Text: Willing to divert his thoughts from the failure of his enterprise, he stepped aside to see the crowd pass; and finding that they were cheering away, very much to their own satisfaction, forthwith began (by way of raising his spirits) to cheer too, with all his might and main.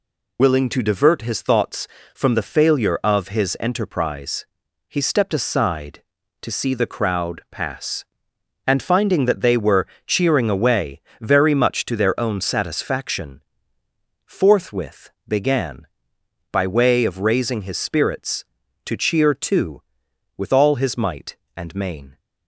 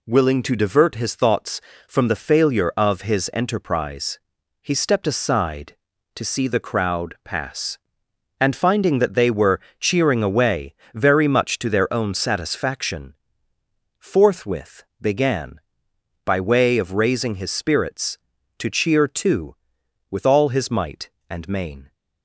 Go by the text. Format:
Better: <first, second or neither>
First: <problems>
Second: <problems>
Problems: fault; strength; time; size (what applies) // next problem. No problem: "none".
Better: second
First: loses the start of "Willing"; at 0.3 s; 75 ms // pauses between "were" and "cheering"; slight; at 9.8 s; 0.18 s long // pauses between "forthwith" and "began"; slight; at 15.0 s; 0.18 s long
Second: pauses between "were" and "cheering"; slight; at 9.5 s; 0.18 s long // pauses between "forthwith" and "began"; slight; at 14.8 s; 0.18 s long